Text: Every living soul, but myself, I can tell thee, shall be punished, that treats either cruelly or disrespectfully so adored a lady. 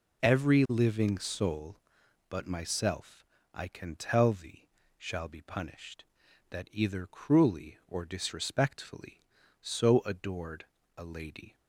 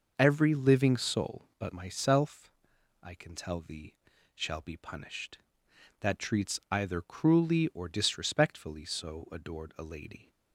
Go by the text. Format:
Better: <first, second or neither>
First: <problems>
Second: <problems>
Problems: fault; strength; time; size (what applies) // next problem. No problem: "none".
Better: second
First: skips "treats"; at 6.6 s // pauses between "adored" and "a"; slight; at 10.6 s; 0.30 s long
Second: none